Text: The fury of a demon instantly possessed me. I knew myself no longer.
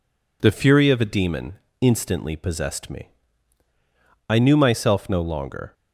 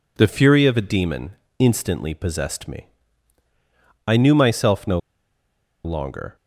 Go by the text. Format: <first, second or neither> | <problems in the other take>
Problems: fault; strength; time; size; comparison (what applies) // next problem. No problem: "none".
first | pauses between "demon" and "instantly"; slight; at 1.3 s; 0.26 s long; slight in the first // pauses between "no" and "longer"; noticeable; at 4.9 s; 0.85 s long